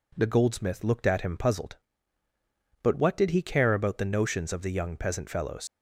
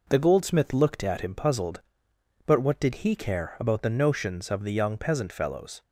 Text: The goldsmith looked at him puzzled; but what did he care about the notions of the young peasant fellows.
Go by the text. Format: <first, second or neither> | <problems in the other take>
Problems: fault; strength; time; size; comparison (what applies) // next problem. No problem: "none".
second | leaves "fellows" unfinished; at 5.6 s; 70 ms